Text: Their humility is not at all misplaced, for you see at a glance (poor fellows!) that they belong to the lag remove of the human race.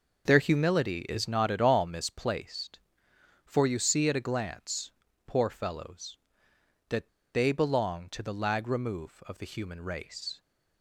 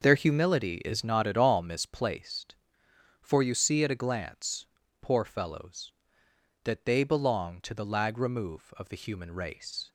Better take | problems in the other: second | pauses between "that" and "they"; slight; at 7.0 s; 0.23 s long

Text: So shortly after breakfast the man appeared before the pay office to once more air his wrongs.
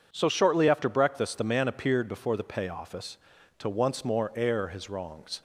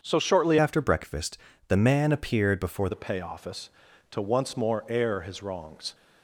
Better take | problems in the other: first | starts louder than the rest; until 1.0 s; 7 dB // changes voice from "after" to "before"; from 0.5 to 2.9 s; 2.4 s long // pauses between "breakfast" and "the"; slight; at 1.3 s; 0.30 s long

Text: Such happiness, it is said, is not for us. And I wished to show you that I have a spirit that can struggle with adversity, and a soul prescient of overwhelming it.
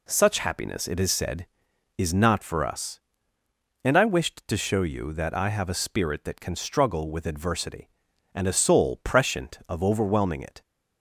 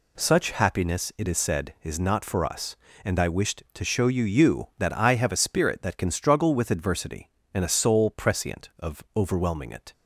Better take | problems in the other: first | says "you" twice; at 4.2 s

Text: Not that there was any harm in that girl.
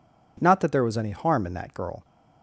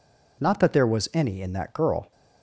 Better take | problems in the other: first | skips "harm"; at 1.4 s

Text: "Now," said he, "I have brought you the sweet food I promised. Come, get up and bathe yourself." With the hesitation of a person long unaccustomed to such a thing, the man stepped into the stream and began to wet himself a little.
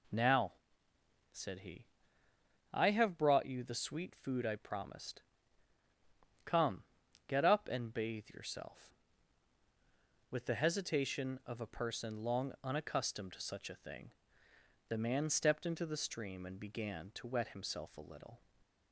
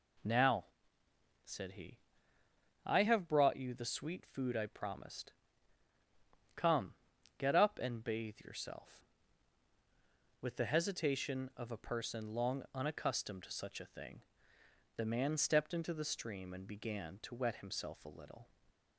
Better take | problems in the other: neither | none

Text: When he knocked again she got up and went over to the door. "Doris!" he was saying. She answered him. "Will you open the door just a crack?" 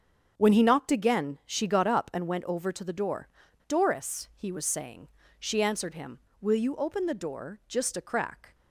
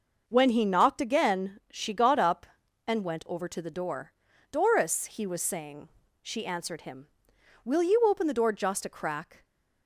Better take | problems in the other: neither | starts louder than the rest; the same in both

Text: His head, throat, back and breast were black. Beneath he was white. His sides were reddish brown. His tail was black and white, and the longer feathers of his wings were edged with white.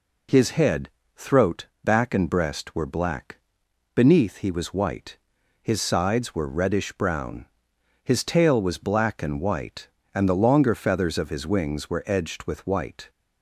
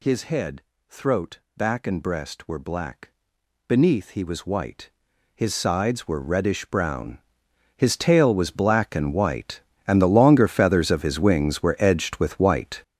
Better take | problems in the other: first | gets louder; strong; throughout; 10.5 dB

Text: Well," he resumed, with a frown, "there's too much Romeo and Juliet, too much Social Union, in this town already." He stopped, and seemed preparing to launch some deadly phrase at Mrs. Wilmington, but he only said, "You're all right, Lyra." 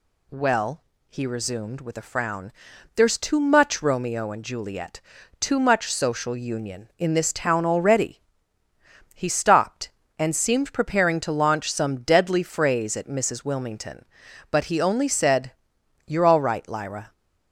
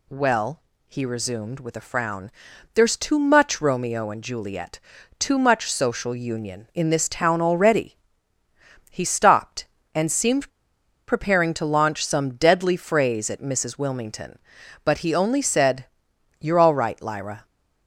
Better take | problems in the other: first | pauses between "seemed" and "preparing"; noticeable; at 10.4 s; 0.60 s long

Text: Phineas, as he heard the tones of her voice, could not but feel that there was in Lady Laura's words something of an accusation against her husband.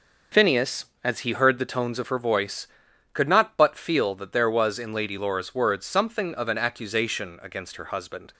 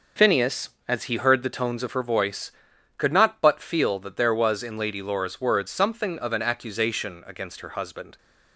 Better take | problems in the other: neither | none

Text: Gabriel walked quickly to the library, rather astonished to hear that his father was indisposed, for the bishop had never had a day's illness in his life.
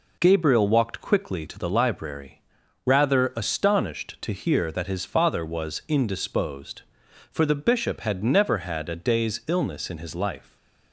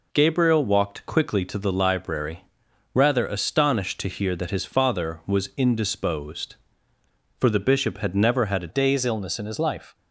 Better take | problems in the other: first | changes voice at "day's"; from 8.6 s on; 1.3 s long

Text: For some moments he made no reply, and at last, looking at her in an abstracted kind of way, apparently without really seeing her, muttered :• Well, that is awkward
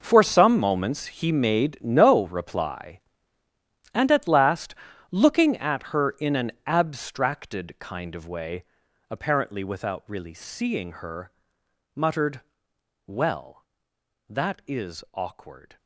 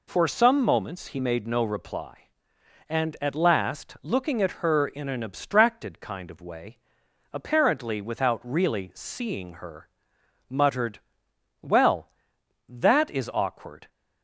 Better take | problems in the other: second | gets quieter; strong; throughout; 15.5 dB

